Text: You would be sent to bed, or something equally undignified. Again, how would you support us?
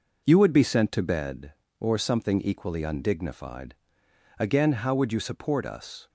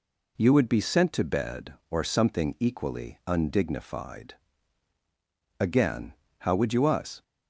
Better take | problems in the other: first | skips "support"; at 6.8 s

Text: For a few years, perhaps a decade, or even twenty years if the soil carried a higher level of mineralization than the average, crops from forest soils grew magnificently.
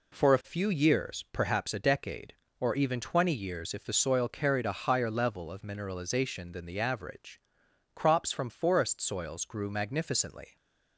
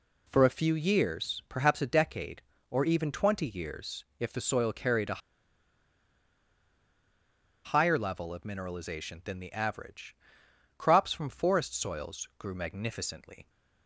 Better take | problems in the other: first | pauses between "years" and "if"; slight; at 4.0 s; 0.16 s long // pauses between "a" and "higher"; strong; at 5.2 s; 2.4 s long

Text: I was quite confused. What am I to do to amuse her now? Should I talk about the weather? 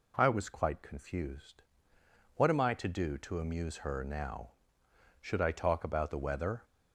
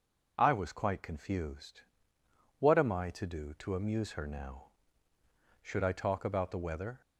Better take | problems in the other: neither | none

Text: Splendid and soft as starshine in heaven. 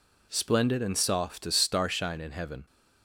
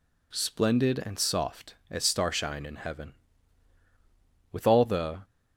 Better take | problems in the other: first | goes on to say "With all the"; noticeable; from 4.5 s on; 0.70 s long

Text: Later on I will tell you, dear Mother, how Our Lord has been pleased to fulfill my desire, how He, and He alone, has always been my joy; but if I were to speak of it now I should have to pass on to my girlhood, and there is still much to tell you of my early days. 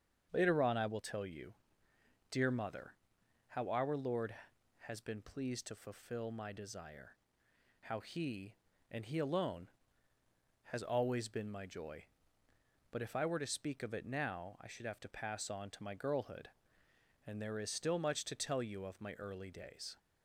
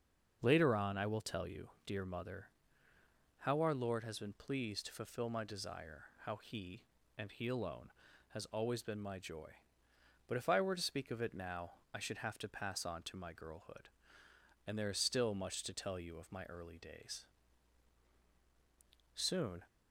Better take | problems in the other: first | starts louder than the rest; until 1.4 s; 6.5 dB; strong in the first // pauses between "now" and "I"; slight; at 11.7 s; 0.20 s long // goes on to say "Soon"; slight; from 19.1 s on; 0.48 s long

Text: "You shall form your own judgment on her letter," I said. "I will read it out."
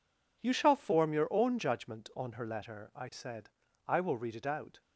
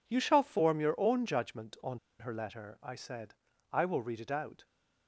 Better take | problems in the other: first | pauses between "on" and "her"; slight; at 1.9 s; 0.20 s long

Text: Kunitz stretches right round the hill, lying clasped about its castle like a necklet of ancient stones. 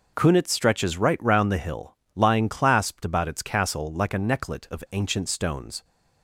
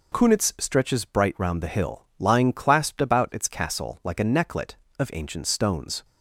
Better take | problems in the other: first | says "bright" for "right"; at 1.0 s

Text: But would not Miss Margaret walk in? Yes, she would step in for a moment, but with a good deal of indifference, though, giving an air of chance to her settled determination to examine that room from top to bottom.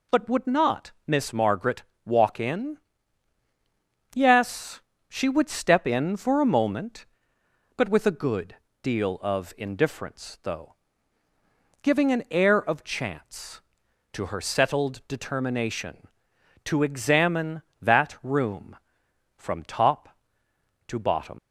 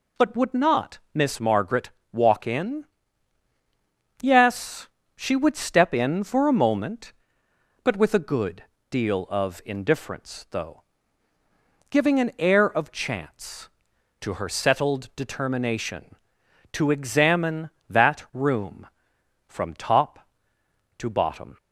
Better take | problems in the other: second | pauses between "not" and "Miss"; slight; at 0.9 s; 0.16 s long; slight in the second // pauses between "Margaret" and "walk"; slight; at 1.8 s; 0.22 s long; slight in the second // pauses between "good" and "deal"; slight; at 8.5 s; 0.26 s long; slight in the second // leaves "bottom" unfinished; at 21.3 s; 75 ms

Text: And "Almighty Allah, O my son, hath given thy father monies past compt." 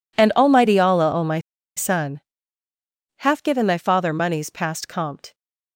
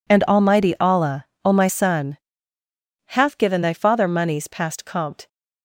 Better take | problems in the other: second | pauses between "my" and "son"; at 1.3 s; 0.37 s long

